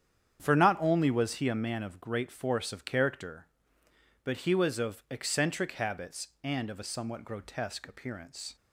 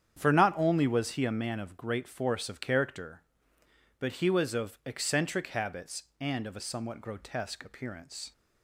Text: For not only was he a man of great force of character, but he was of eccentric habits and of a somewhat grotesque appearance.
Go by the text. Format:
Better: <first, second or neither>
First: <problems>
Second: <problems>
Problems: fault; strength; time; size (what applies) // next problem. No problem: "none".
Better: neither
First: starts louder than the rest; strong; until 1.4 s; 8.5 dB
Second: starts louder than the rest; strong; until 1.2 s; 8.5 dB